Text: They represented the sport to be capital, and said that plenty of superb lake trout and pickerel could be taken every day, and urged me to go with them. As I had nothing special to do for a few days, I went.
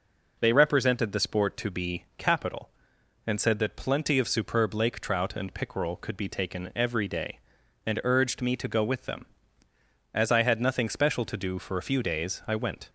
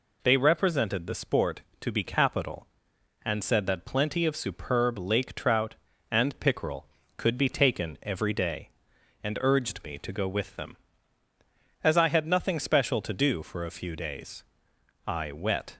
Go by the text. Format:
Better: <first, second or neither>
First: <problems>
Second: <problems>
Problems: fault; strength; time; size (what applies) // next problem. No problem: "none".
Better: first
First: none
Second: says "wet" for "went"; at 15.3 s